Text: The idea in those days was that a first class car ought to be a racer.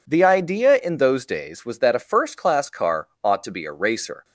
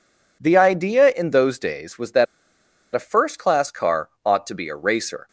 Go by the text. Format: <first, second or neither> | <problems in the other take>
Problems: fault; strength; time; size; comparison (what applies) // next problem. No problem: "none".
first | pauses between "that" and "a"; noticeable; at 2.2 s; 0.69 s long